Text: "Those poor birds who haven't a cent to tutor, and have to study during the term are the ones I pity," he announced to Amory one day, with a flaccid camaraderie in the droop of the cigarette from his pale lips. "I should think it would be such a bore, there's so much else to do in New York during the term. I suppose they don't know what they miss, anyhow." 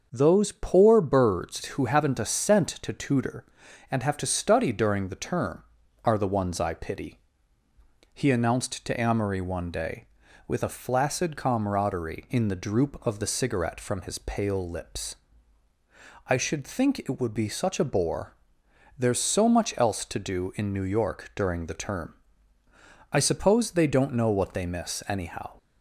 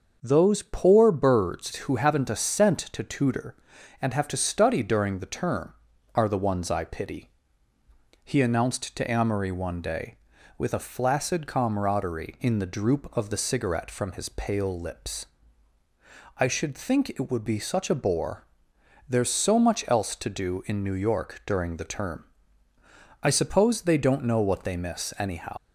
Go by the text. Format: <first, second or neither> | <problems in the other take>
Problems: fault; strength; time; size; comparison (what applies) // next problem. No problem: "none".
first | starts louder than the rest; noticeable; until 1.2 s; 6 dB; noticeable in the first // leaves "anyhow" unfinished; at 25.5 s; 105 ms